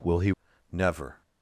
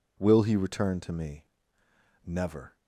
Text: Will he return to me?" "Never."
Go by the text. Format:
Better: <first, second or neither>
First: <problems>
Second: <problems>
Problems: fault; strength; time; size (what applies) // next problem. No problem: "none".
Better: second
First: skips "return to me"; at 0.5 s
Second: none